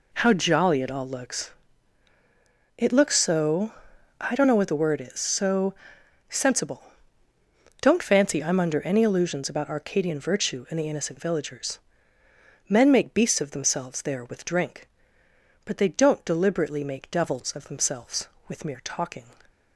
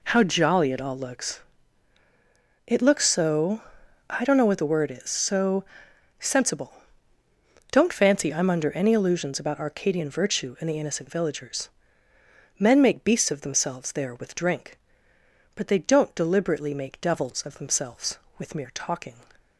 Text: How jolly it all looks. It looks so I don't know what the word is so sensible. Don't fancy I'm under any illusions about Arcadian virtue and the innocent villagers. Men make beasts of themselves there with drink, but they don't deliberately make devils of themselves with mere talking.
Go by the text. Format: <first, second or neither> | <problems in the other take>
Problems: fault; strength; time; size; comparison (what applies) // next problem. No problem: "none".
neither | pauses between "so" and "I"; noticeable; the same in both // pauses between "so" and "sensible"; noticeable; the same in both